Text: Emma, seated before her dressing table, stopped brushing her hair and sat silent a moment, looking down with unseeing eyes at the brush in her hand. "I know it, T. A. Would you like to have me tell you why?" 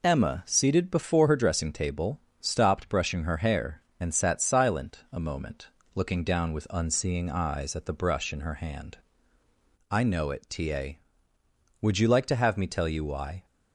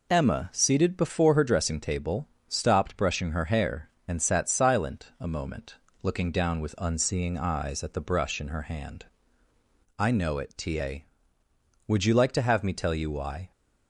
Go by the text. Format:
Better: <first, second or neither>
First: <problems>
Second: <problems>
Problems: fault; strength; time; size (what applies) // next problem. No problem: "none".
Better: neither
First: none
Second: none